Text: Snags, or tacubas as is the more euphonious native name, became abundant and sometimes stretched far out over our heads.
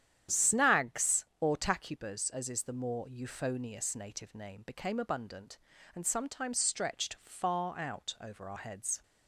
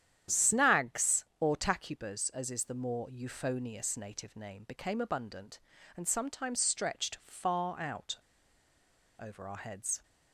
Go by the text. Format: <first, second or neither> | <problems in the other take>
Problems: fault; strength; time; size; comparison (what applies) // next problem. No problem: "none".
first | starts louder than the rest; strong; until 1.4 s; 9.5 dB; strong in the first // pauses between "out" and "over"; at 8.1 s; 1.0 s long